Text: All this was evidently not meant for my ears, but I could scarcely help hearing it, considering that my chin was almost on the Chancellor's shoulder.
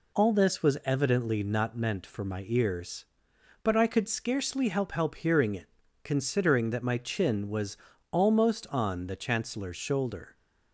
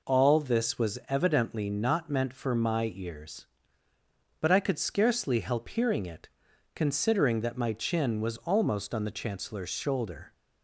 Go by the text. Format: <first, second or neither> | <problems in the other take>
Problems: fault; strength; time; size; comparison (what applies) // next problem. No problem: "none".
second | says "help" twice; at 4.9 s // pauses between "was" and "almost"; slight; at 7.7 s; 0.34 s long